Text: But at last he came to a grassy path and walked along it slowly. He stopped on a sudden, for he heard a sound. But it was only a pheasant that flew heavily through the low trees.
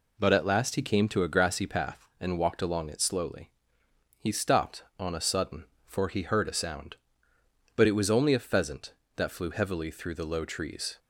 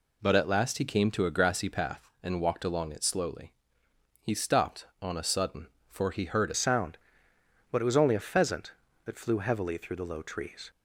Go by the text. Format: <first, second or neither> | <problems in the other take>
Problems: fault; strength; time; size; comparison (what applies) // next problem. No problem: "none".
first | changes voice at "sound"; from 6.5 s on; 4.2 s long